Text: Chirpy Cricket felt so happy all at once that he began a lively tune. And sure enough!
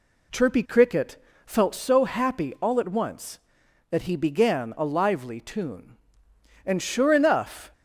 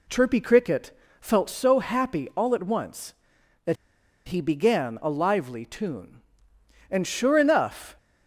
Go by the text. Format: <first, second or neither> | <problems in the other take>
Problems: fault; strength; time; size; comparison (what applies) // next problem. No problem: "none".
first | pauses between "Cricket" and "felt"; slight; at 0.9 s; 0.30 s long; slight in the first // pauses between "that" and "he"; noticeable; at 3.7 s; 0.51 s long